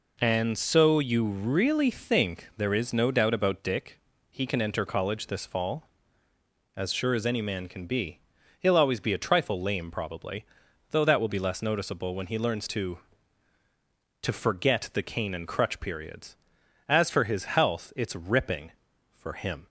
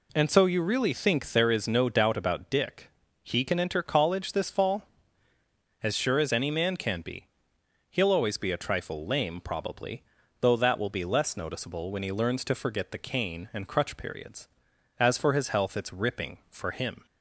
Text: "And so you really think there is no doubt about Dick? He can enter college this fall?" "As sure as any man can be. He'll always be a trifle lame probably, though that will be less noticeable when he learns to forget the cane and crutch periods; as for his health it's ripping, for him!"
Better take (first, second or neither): second